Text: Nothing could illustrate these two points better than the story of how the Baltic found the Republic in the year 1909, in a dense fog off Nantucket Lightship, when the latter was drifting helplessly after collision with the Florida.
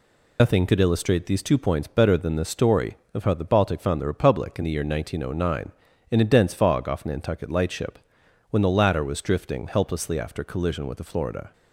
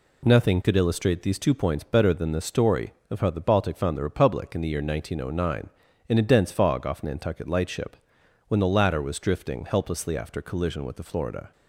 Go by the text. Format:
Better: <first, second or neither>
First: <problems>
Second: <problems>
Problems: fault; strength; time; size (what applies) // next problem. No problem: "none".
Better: second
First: loses the start of "Nothing"; at 0.3 s; 115 ms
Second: none